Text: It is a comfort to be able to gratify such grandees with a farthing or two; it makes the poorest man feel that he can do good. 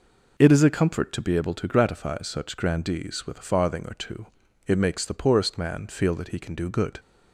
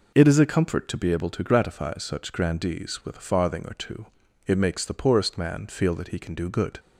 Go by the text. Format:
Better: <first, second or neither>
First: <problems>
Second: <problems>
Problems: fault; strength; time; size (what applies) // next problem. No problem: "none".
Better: neither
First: none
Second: none